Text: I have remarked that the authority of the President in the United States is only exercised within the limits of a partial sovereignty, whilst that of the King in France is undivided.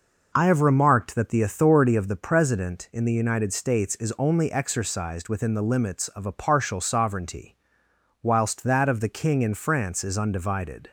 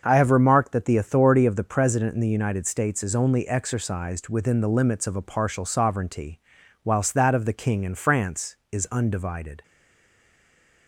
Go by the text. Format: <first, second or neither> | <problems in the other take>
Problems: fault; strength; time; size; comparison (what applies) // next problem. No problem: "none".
first | starts louder than the rest; until 1.0 s; 6.5 dB // stays silent after the last word; noticeable; from 9.6 s on; 1.2 s long